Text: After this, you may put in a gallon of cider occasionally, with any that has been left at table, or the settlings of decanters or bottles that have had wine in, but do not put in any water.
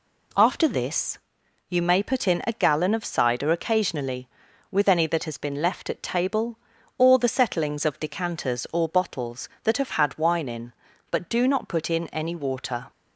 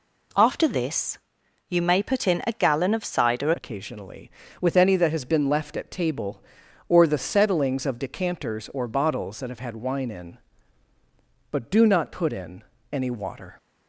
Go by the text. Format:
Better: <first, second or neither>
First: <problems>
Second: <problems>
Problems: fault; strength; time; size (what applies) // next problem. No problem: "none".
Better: first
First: none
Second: changes voice at "occasionally"; from 3.5 s on; 10.0 s long // pauses between "in" and "any"; slight; at 12.6 s; 0.30 s long